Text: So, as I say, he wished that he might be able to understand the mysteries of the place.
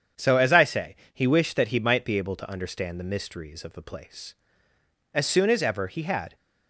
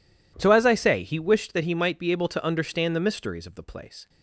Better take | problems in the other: second | starts louder than the rest; strong; until 1.3 s; 8 dB // goes on to say "As soon as ever he had"; noticeable; from 5.1 s on; 1.2 s long

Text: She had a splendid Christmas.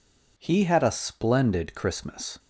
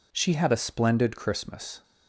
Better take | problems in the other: second | says "He" for "She"; at 0.3 s

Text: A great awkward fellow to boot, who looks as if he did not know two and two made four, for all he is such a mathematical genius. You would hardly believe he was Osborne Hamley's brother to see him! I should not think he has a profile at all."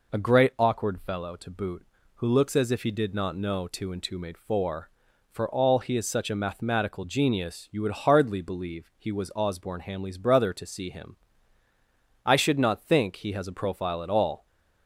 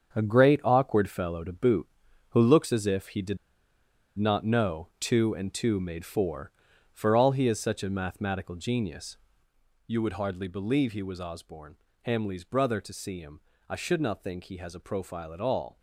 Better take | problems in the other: first | starts louder than the rest; strong; until 1.1 s; 7 dB // pauses between "did" and "not"; noticeable; at 3.3 s; 0.81 s long // pauses between "Osborne" and "Hamley's"; slight; at 11.7 s; 0.30 s long

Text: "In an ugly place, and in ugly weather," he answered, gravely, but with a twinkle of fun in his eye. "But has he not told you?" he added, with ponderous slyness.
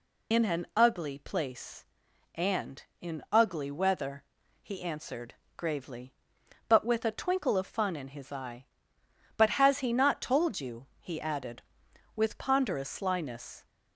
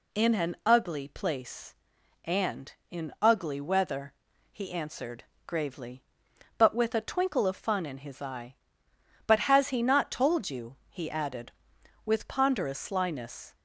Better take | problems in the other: second | loses the start of "In"; at 0.3 s; 75 ms

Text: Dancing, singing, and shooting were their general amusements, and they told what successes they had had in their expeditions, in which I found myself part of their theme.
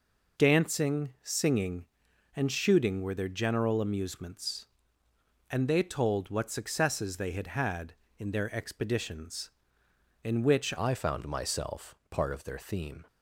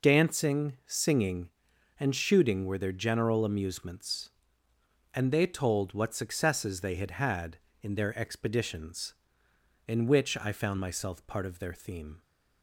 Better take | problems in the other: second | changes voice at "I"; from 10.7 s on; 2.3 s long

